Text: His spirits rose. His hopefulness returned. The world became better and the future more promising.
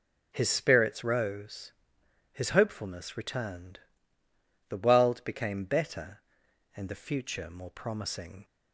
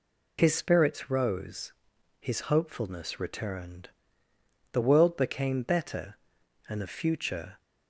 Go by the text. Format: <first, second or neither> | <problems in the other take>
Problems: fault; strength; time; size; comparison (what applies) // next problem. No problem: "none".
first | stops before "more promising"; at 7.5 s